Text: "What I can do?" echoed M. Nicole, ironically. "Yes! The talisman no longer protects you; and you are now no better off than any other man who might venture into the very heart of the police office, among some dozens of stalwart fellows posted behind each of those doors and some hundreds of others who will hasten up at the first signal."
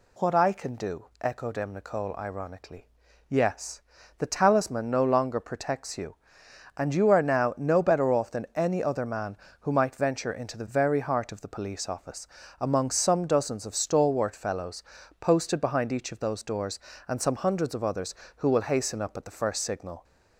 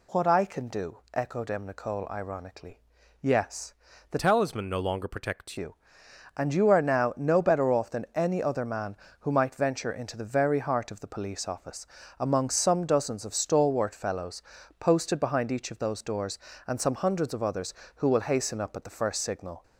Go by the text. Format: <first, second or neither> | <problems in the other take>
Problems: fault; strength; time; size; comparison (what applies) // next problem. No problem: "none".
first | changes voice from "talisman" to "protects"; from 4.1 to 5.5 s; 1.4 s long // pauses between "fellows" and "posted"; at 14.4 s; 0.38 s long; also in the first